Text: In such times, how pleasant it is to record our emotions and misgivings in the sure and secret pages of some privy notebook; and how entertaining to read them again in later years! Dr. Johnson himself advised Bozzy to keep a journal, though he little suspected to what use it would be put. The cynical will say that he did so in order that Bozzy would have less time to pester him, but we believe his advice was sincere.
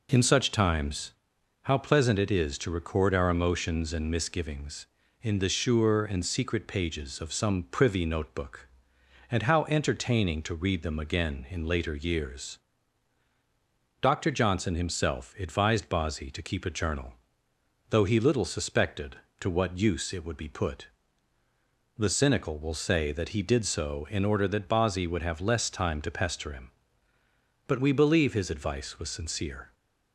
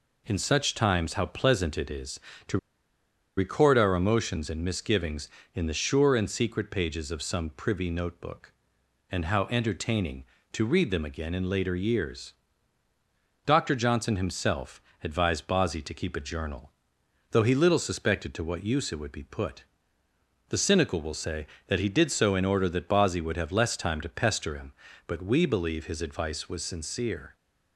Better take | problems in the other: first | pauses between "to" and "record"; noticeable; at 2.5 s; 0.80 s long // pauses between "himself" and "advised"; slight; at 14.8 s; 0.22 s long

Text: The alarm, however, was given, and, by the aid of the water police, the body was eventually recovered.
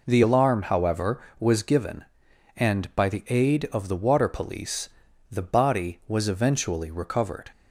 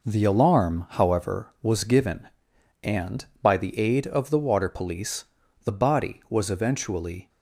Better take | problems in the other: first | stops before "recovered"; at 7.2 s

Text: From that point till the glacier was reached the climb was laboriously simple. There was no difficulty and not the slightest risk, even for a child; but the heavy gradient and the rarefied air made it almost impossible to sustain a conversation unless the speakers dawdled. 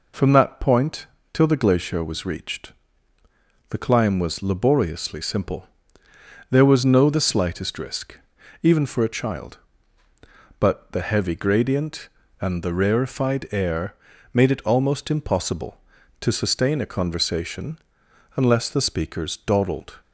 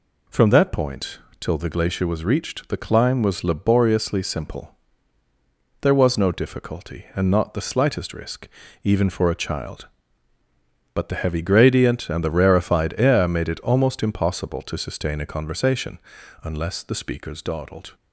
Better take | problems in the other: second | pauses between "point" and "till"; slight; at 1.0 s; 0.26 s long; slight in the second // pauses between "reached" and "the"; at 2.7 s; 1.0 s long // skips "difficulty and not"; at 7.0 s // pauses between "air" and "made"; at 13.9 s; 0.40 s long // pauses between "conversation" and "unless"; noticeable; at 17.7 s; 0.58 s long; noticeable in the second

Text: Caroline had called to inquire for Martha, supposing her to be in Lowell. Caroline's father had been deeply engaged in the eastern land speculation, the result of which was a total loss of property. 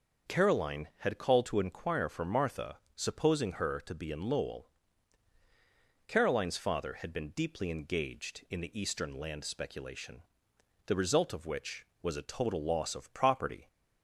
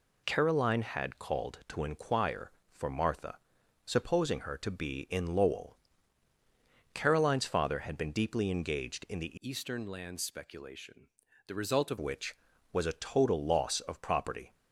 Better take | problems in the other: first | changes voice from "eastern" to "of"; from 9.3 to 11.9 s; 2.6 s long

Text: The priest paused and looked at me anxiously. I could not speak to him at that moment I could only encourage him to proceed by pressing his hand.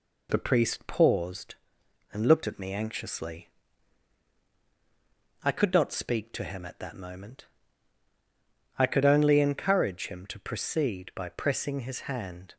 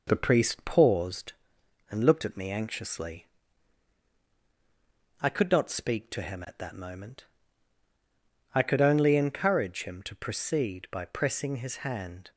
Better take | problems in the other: first | starts louder than the rest; noticeable; until 1.7 s; 5 dB // pauses between "moment" and "I"; strong; at 7.2 s; 1.2 s long; strong in the first

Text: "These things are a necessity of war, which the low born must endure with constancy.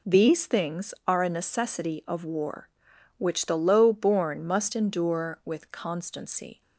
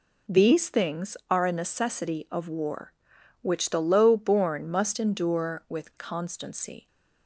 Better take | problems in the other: neither | none

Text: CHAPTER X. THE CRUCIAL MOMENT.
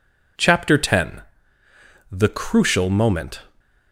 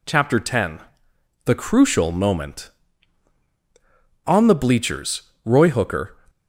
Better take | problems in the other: first | goes on to say "On the bleachers Roy Hooker"; strong; from 4.2 s on; 1.9 s long

